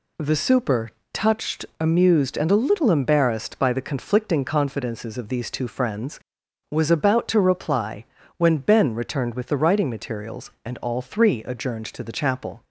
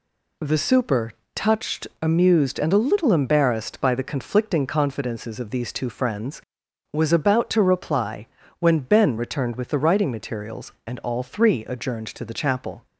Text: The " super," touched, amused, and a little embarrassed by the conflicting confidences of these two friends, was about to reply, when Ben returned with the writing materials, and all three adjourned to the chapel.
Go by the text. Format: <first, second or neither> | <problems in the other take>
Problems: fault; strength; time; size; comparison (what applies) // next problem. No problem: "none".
neither | none